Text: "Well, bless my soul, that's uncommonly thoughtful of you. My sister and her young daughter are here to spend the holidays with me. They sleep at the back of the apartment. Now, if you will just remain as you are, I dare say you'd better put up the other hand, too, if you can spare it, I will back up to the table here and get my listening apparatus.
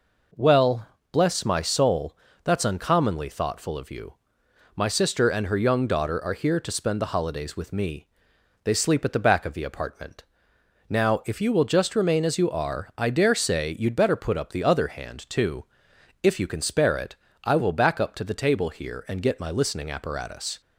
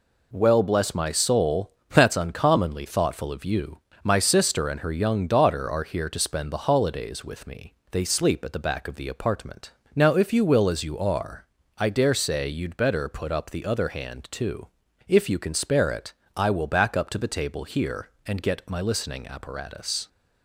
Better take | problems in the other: first | skips "just remain"; at 10.6 s

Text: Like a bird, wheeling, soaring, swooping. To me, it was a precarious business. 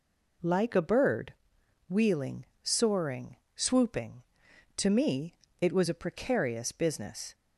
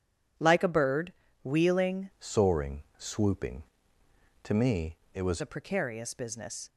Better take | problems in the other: first | changes voice from "soaring" to "was"; from 2.1 to 5.4 s; 3.3 s long

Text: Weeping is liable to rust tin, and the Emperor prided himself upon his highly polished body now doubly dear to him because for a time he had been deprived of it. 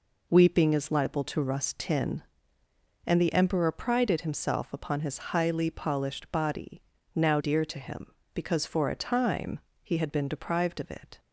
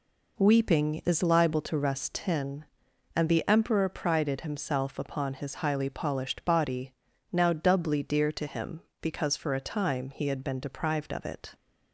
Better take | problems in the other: second | pauses between "body" and "now"; slight; at 6.8 s; 0.34 s long; also in the second // skips "doubly"; at 7.3 s // pauses between "time" and "he"; slight; at 9.5 s; 0.24 s long

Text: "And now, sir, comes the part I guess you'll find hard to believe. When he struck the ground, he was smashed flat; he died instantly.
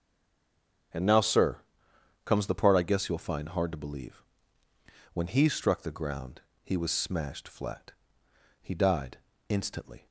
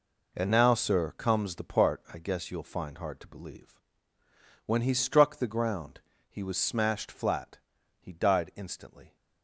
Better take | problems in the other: second | stays silent before the first word; slight; until 0.9 s; 0.9 s long // starts louder than the rest; until 2.5 s; 7 dB // pauses between "died" and "instantly"; slight; at 9.1 s; 0.30 s long

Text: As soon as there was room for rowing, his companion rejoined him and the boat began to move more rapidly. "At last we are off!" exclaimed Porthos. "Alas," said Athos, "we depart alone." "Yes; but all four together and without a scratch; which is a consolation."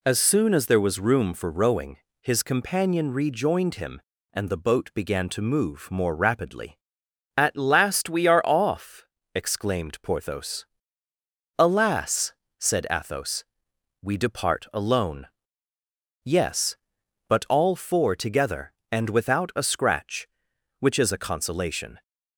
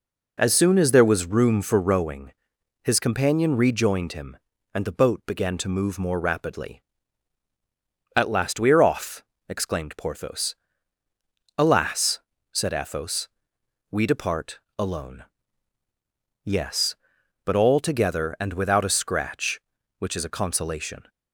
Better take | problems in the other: first | pauses between "depart" and "alone"; slight; at 14.6 s; 0.18 s long // skips "four"; at 17.8 s

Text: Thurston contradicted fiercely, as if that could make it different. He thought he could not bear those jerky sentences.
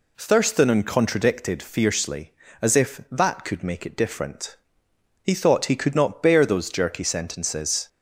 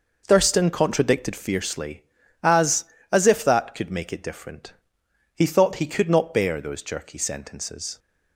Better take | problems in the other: first | says "as" twice; at 3.1 s

